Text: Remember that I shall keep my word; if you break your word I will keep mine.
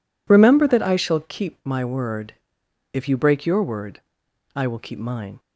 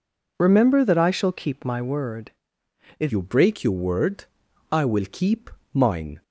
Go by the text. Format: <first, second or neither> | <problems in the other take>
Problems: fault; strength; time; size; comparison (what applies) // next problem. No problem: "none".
first | changes voice at "you"; from 3.1 s on; 3.1 s long // pauses between "word" and "I"; noticeable; at 4.2 s; 0.46 s long; noticeable in the first // pauses between "keep" and "mine"; slight; at 5.5 s; 0.24 s long